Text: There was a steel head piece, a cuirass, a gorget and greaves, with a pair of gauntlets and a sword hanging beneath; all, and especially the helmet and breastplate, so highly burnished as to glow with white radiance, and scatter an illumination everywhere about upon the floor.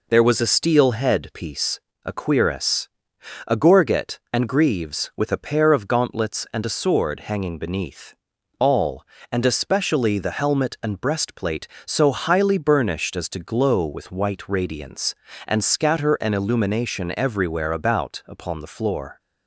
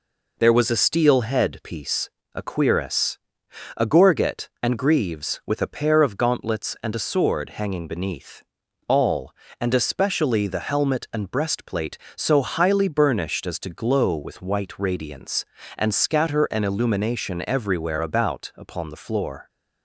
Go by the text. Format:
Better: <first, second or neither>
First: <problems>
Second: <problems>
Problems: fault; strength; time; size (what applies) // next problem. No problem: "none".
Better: neither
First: none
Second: none